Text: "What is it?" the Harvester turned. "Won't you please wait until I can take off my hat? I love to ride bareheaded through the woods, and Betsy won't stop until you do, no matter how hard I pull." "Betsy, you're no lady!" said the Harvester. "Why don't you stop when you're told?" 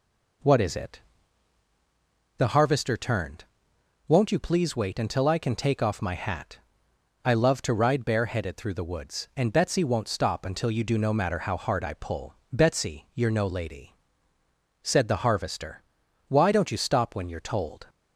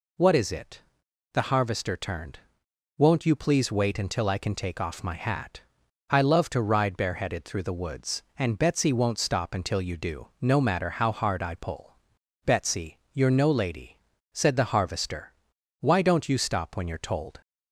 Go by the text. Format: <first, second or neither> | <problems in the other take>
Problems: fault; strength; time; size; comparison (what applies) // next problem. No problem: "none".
neither | none